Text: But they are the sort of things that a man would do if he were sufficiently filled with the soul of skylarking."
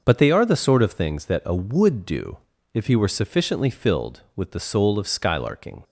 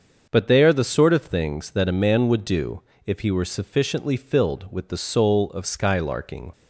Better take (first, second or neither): second